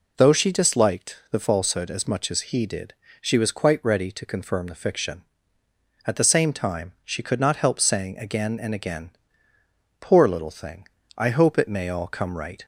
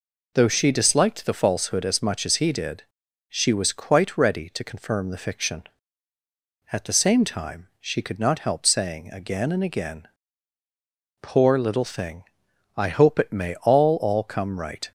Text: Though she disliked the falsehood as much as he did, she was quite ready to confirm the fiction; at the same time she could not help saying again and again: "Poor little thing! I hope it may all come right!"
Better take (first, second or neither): first